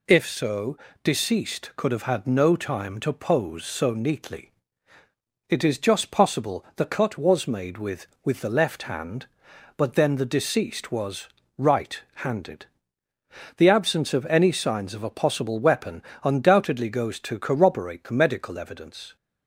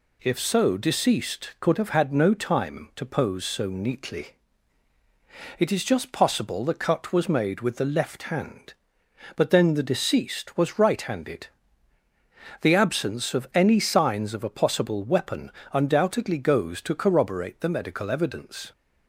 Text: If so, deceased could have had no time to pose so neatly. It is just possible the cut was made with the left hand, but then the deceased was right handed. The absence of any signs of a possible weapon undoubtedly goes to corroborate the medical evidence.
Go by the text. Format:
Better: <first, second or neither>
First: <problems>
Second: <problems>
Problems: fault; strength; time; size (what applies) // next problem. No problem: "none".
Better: second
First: says "with" twice; at 8.2 s // pauses between "was" and "right"; slight; at 11.2 s; 0.30 s long // pauses between "right" and "handed"; slight; at 11.9 s; 0.16 s long // pauses between "weapon" and "undoubtedly"; slight; at 16.0 s; 0.20 s long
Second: pauses between "weapon" and "undoubtedly"; slight; at 15.5 s; 0.20 s long